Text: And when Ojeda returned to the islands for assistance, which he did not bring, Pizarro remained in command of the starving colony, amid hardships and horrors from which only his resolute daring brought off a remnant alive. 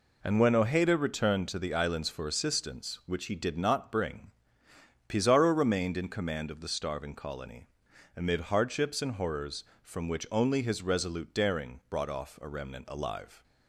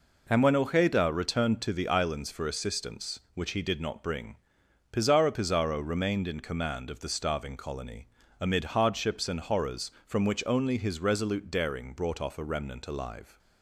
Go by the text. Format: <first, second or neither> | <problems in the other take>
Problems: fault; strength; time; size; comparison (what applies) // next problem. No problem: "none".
first | says "Pizarro" twice; at 5.3 s